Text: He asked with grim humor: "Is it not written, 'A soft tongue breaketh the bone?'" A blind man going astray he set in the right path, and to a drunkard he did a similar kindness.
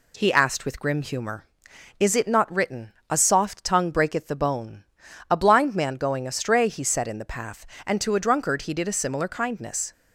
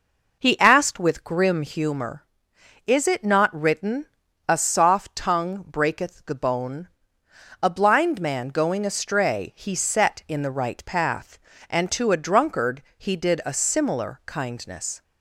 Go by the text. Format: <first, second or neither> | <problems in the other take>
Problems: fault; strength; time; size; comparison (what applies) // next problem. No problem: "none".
second | skips "right"; at 7.3 s